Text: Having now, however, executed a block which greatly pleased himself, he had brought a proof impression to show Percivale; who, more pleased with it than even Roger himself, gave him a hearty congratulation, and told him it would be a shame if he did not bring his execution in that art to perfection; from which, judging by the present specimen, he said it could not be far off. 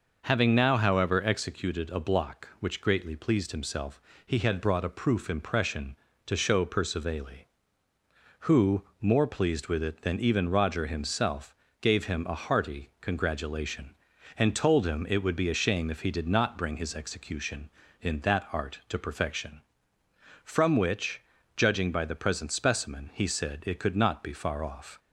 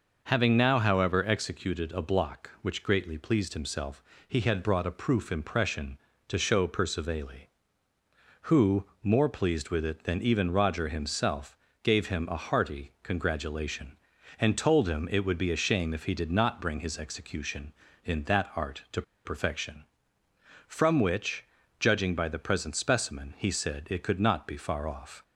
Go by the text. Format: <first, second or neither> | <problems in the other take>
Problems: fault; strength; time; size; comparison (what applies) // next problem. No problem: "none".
first | pauses between "to" and "perfection"; slight; at 19.0 s; 0.22 s long